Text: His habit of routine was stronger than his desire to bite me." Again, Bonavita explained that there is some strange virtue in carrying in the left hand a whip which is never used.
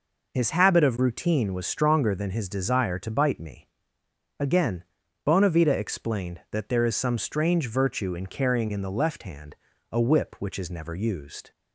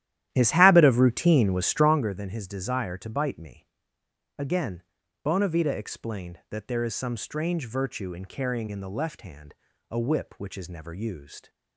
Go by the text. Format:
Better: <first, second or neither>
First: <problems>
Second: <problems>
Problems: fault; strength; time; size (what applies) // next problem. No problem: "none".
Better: first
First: pauses between "hand" and "a"; slight; at 9.5 s; 0.36 s long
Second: starts louder than the rest; strong; until 2.1 s; 12.5 dB // pauses between "hand" and "a"; slight; at 9.5 s; 0.36 s long